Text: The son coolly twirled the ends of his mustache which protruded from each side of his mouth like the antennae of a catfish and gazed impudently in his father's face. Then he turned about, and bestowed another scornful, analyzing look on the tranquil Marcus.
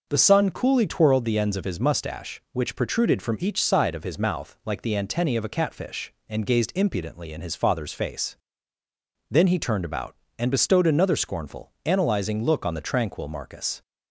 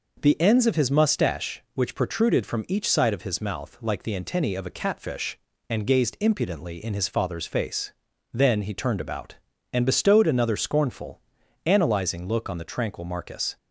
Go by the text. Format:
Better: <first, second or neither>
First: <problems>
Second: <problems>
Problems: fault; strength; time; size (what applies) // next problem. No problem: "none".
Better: first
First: none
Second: skips "son coolly twirled the"; at 0.4 s